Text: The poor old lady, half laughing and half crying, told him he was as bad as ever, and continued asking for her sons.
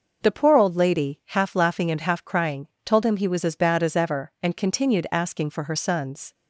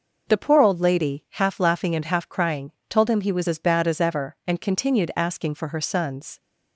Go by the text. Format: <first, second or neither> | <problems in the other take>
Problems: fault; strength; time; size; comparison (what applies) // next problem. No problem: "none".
neither | none